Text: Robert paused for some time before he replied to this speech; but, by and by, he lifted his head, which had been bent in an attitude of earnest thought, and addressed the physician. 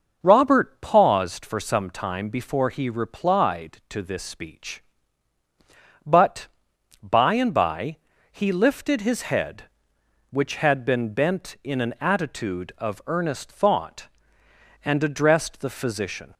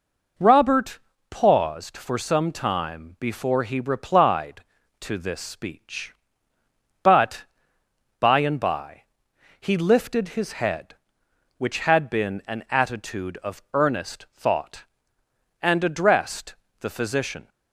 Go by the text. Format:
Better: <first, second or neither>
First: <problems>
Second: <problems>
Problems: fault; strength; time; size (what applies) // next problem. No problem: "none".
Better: first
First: none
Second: pauses between "Robert" and "paused"; slight; at 0.9 s; 0.32 s long // skips "bent in"; at 12.4 s // pauses between "addressed" and "the"; slight; at 16.5 s; 0.28 s long